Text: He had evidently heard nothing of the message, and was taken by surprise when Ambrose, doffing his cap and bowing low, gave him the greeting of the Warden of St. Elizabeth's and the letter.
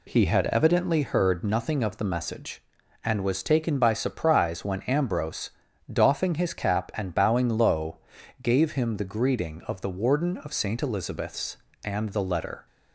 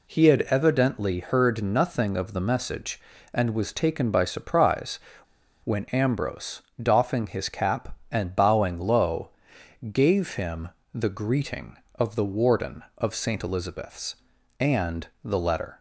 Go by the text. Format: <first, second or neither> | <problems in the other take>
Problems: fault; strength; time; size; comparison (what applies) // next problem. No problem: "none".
first | pauses between "surprise" and "when"; noticeable; at 4.9 s; 0.65 s long // pauses between "him" and "the"; slight; at 10.6 s; 0.24 s long // pauses between "and" and "the"; slight; at 15.0 s; 0.18 s long